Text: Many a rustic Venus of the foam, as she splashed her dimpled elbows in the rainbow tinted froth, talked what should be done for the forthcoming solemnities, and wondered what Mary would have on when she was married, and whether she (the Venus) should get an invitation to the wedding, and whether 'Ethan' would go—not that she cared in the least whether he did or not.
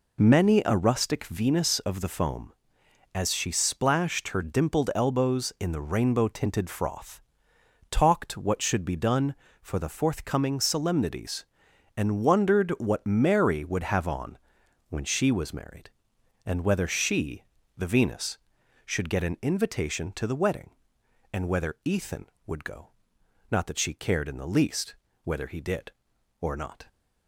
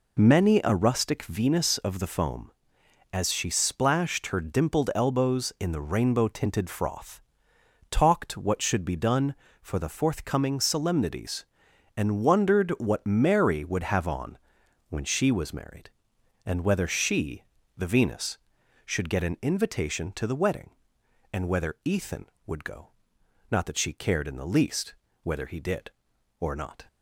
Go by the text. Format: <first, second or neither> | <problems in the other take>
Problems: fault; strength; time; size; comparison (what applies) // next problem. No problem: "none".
neither | pauses between "on" and "when"; noticeable; the same in both // pauses between "least" and "whether"; slight; the same in both